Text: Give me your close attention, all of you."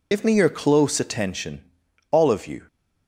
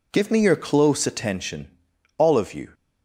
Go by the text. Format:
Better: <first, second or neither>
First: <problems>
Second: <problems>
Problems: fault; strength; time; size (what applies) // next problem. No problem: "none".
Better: second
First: loses the start of "Give"; at 0.1 s; 55 ms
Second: none